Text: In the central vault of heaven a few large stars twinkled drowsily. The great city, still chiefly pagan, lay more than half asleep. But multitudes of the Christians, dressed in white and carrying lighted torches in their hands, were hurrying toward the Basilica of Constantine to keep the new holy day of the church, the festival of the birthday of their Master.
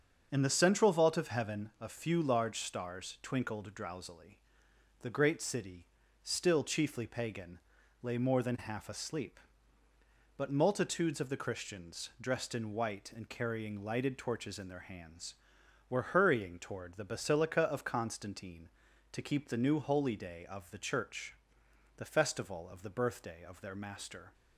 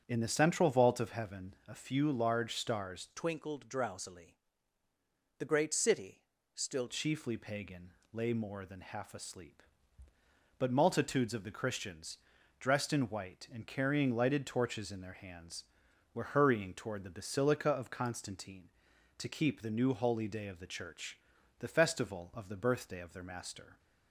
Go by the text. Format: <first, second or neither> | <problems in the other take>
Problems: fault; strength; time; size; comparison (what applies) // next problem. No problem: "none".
first | starts louder than the rest; strong; until 1.0 s; 8 dB; also in the first // changes voice from "twinkled" to "still"; from 3.1 to 6.8 s; 3.7 s long